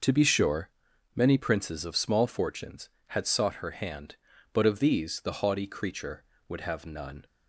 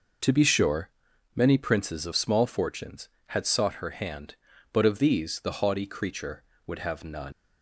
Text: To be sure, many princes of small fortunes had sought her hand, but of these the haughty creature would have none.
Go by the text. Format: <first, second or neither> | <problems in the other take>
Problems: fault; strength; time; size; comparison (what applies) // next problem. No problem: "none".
first | leaves "none" unfinished; at 7.3 s; 110 ms